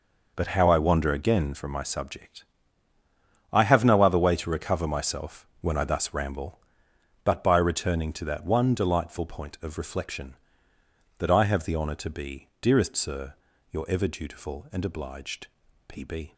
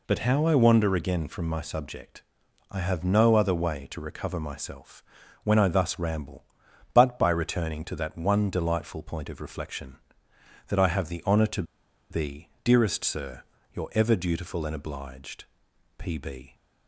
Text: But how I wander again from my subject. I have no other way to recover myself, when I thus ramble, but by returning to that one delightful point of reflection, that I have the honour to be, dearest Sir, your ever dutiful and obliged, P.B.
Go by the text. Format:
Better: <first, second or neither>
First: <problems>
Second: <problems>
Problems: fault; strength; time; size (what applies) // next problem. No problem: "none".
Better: first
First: none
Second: pauses between "to" and "be"; noticeable; at 11.6 s; 0.47 s long